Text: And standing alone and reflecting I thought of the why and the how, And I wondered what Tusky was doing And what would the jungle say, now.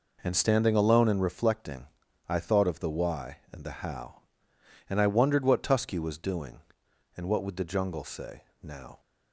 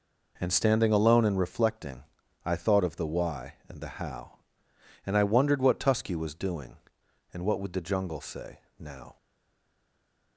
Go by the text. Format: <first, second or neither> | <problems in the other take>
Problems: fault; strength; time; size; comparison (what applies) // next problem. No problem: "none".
first | pauses between "reflecting" and "I"; at 2.0 s; 0.42 s long; also in the first // stays silent after the last word; noticeable; from 9.1 s on; 1.2 s long